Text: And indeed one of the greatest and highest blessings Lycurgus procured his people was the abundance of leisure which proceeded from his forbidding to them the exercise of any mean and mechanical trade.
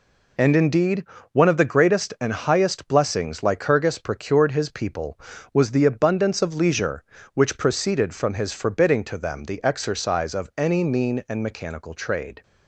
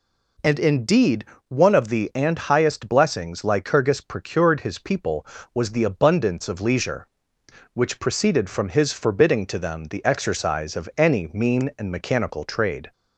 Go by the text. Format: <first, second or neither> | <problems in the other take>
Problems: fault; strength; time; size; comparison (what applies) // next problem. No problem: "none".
first | pauses between "indeed" and "one"; slight; at 1.2 s; 0.22 s long; slight in the first // skips "greatest"; at 2.1 s